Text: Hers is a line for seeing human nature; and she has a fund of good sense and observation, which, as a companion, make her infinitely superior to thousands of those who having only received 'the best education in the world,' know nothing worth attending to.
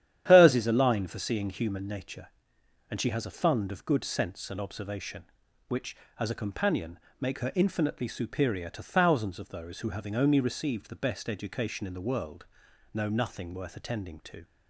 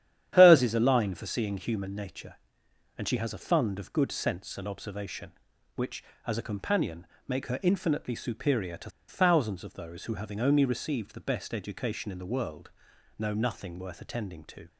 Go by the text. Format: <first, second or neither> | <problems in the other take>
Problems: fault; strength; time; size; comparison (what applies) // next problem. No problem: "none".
first | starts louder than the rest; strong; until 1.3 s; 10.5 dB; strong in the first // pauses between "to" and "thousands"; slight; at 8.8 s; 0.18 s long